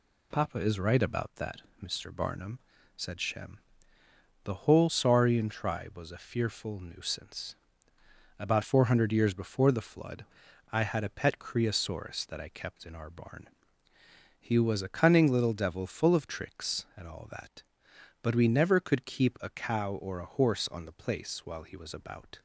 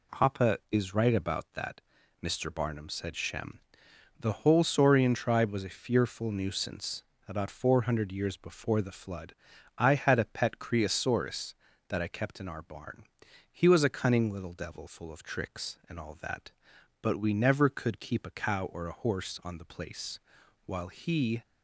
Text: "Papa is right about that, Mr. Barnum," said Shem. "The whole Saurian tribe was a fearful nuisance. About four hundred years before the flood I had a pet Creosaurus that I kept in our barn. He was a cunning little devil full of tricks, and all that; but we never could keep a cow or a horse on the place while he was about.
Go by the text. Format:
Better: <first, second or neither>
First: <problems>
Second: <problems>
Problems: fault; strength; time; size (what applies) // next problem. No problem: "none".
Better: first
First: pauses between "flood" and "I"; noticeable; at 10.2 s; 0.46 s long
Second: pauses between "flood" and "I"; at 9.3 s; 0.42 s long // pauses between "place" and "while"; noticeable; at 20.1 s; 0.49 s long // stops before "was about"; at 21.4 s